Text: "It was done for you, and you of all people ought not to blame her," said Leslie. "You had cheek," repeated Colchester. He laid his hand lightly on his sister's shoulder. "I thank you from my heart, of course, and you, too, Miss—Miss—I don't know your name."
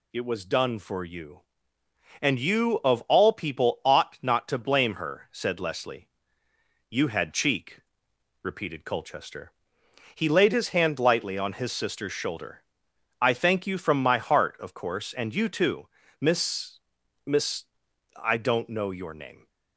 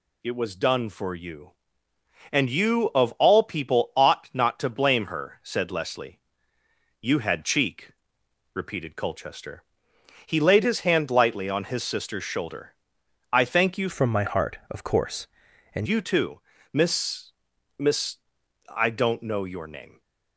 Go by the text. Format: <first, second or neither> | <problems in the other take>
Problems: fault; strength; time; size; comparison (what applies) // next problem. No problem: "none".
first | changes voice from "from" to "and"; from 13.8 to 15.8 s; 2.0 s long